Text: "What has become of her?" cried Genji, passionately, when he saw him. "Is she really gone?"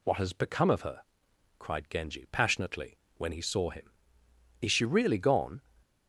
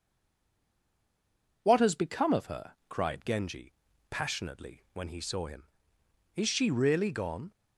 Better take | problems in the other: first | stays silent before the first word; noticeable; until 1.6 s; 1.6 s long

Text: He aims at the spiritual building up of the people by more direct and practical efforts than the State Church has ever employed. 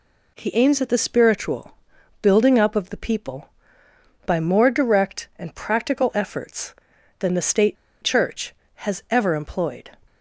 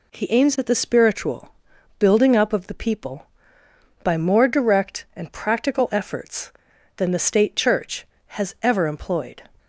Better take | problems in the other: second | pauses between "spiritual" and "building"; at 1.7 s; 0.44 s long; also in the second // pauses between "State" and "Church"; slight; at 7.7 s; 0.26 s long

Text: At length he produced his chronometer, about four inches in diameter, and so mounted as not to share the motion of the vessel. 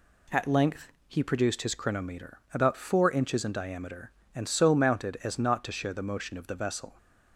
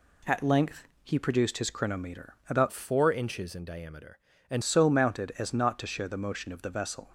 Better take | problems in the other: first | pauses between "length" and "he"; slight; at 0.8 s; 0.16 s long; slight in the first // changes voice from "four" to "and"; from 2.7 to 4.6 s; 1.9 s long

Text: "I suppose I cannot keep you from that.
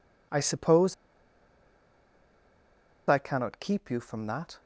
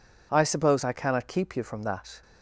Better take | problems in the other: second | pauses between "suppose" and "I"; strong; at 0.9 s; 2.1 s long

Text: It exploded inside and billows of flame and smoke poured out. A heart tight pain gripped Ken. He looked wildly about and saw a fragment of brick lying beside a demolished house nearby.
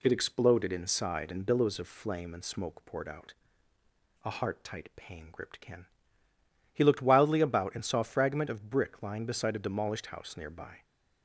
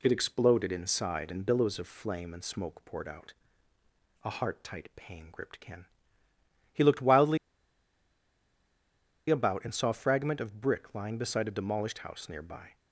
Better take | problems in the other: first | pauses between "wildly" and "about"; strong; at 7.3 s; 1.9 s long

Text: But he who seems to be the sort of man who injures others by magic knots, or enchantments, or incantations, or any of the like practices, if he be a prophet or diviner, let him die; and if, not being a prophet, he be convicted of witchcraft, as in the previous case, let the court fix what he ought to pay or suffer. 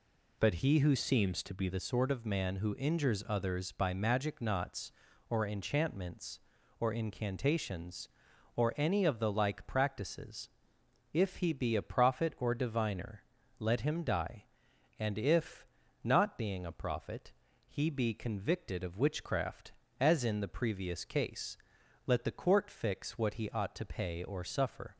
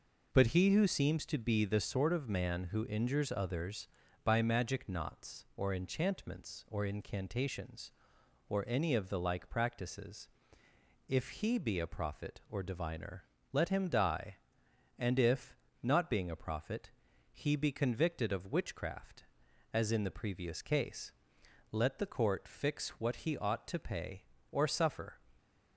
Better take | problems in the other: second | changes voice from "seems" to "be"; from 0.9 to 1.6 s; 0.7 s long

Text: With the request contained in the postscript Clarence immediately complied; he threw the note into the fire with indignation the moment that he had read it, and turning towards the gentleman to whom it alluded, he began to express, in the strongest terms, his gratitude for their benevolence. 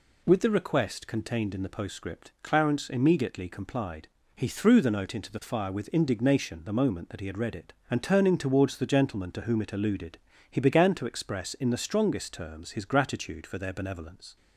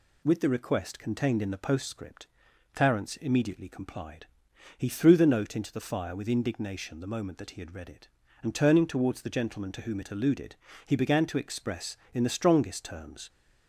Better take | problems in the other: first | pauses between "postscript" and "Clarence"; noticeable; at 2.2 s; 0.48 s long // stops before "his gratitude for their benevolence"; at 13.2 s

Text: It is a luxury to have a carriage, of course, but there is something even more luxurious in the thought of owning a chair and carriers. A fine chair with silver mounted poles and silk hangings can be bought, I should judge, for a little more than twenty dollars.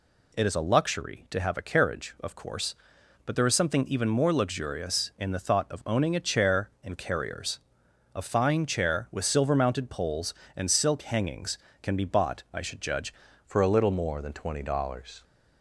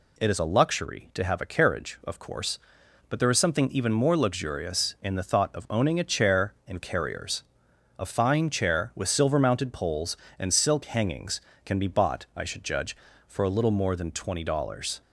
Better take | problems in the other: second | changes voice at "for"; from 13.4 s on; 1.8 s long

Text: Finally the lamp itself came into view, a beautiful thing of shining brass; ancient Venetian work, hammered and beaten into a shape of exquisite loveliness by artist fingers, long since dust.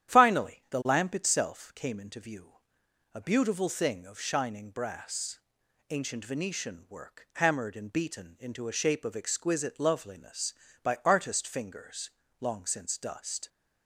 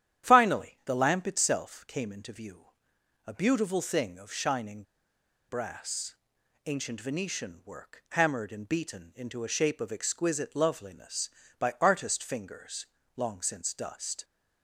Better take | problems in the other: first | starts louder than the rest; strong; until 1.3 s; 10.5 dB; strong in the first // pauses between "shining" and "brass"; noticeable; at 4.8 s; 0.66 s long

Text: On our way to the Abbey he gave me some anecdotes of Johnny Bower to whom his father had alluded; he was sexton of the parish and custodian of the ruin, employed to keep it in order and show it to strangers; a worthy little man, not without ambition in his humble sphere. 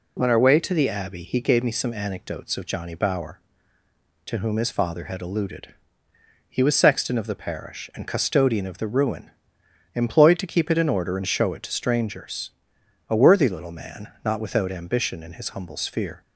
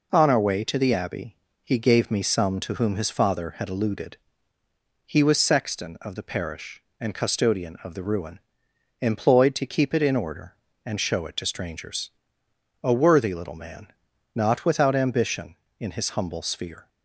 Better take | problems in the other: first | pauses between "Abbey" and "he"; slight; at 1.3 s; 0.28 s long // skips "anecdotes of Johnny Bower"; at 2.6 s

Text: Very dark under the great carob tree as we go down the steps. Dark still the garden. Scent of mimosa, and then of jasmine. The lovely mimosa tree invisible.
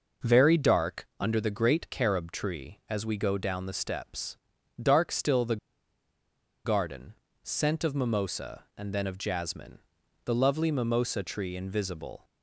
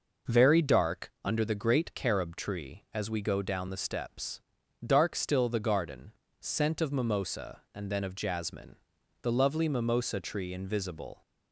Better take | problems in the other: second | pauses between "the" and "garden"; at 5.5 s; 1.0 s long

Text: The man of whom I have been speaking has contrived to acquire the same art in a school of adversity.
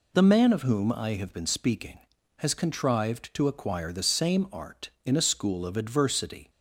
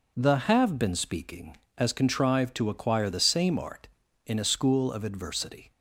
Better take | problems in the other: first | skips "man of whom I"; at 0.4 s

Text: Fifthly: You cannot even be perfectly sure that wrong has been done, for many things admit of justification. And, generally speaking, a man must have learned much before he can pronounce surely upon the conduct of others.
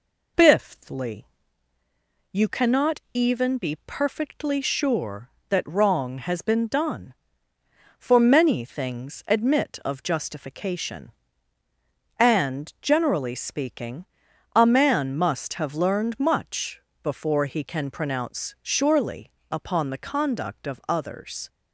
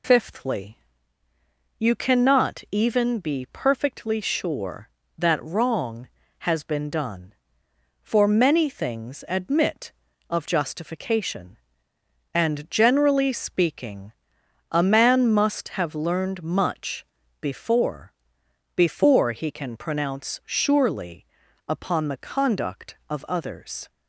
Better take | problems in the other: first | pauses between "much" and "before"; at 17.0 s; 0.38 s long; slight in the first // says "before" twice; at 18.7 s // pauses between "surely" and "upon"; at 21.2 s; 0.42 s long; slight in the first

